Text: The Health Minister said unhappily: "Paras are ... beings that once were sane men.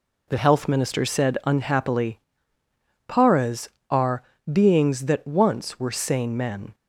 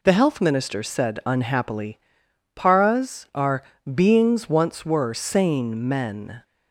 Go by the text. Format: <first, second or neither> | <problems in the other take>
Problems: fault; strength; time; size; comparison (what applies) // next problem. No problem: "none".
first | skips "that"; at 4.4 s